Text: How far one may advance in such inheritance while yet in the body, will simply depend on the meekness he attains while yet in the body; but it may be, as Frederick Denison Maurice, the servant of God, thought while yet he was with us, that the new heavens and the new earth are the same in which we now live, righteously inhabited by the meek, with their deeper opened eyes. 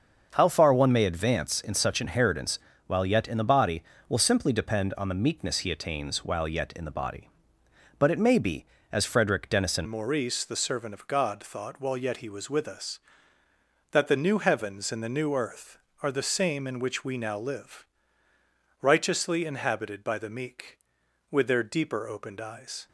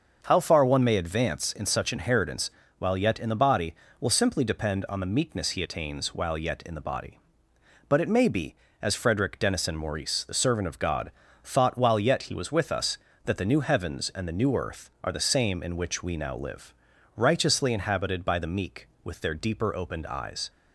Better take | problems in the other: second | starts louder than the rest; until 1.3 s; 6.5 dB; also in the second // pauses between "inheritance" and "while"; slight; at 2.5 s; 0.30 s long; slight in the second // changes voice at "Maurice"; from 9.8 s on; 13.0 s long

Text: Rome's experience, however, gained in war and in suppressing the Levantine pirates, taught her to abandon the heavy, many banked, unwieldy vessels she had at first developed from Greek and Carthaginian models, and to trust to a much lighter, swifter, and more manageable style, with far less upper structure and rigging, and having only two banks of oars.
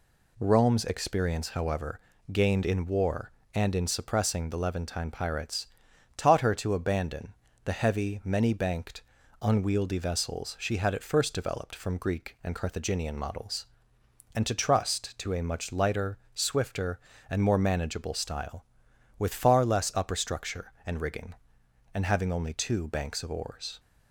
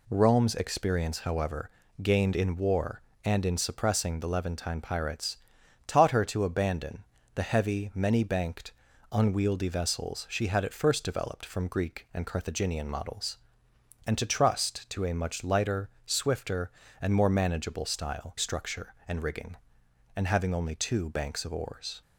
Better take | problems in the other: first | pauses between "abandon" and "the"; slight; at 7.0 s; 0.30 s long; slight in the first // skips "with far less upper"; at 18.3 s

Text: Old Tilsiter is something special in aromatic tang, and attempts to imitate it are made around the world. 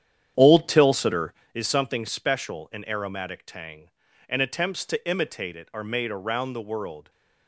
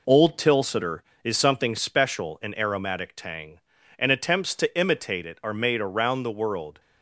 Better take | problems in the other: second | starts louder than the rest; strong; until 1.5 s; 9.5 dB

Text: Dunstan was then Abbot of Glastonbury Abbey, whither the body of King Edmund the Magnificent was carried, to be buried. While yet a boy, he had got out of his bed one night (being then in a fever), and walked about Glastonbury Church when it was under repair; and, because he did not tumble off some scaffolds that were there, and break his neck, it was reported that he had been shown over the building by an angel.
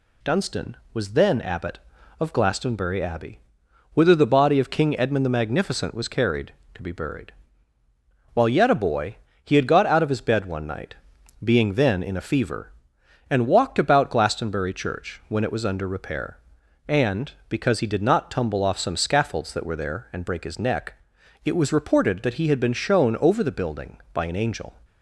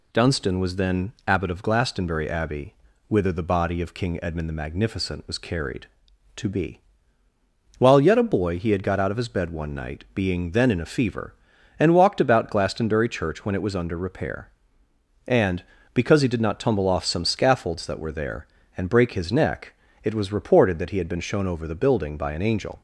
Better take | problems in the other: first | skips "buried"; at 7.2 s

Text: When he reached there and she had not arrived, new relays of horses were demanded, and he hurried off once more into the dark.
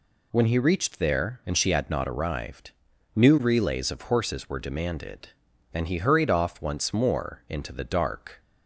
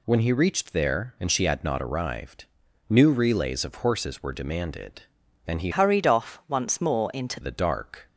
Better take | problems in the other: first | changes voice from "hurried" to "into"; from 5.7 to 7.3 s; 1.6 s long

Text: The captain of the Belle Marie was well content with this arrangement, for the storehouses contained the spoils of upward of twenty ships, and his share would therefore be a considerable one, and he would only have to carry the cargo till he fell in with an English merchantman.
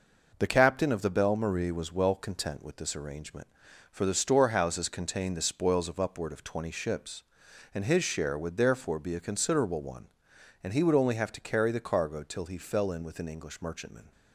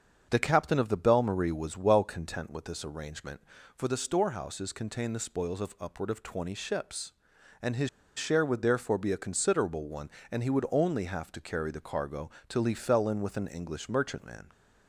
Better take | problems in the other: first | starts louder than the rest; until 1.3 s; 7 dB // pauses between "his" and "share"; slight; at 7.8 s; 0.27 s long // pauses between "cargo" and "till"; slight; at 12.2 s; 0.18 s long

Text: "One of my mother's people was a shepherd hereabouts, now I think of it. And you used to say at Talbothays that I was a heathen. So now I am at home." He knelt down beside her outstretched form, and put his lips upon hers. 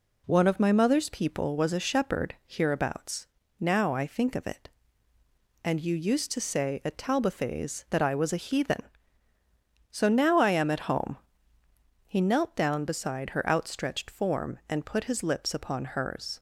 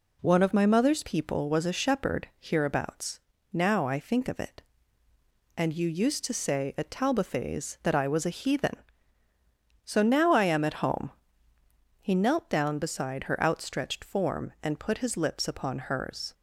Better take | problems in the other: neither | none

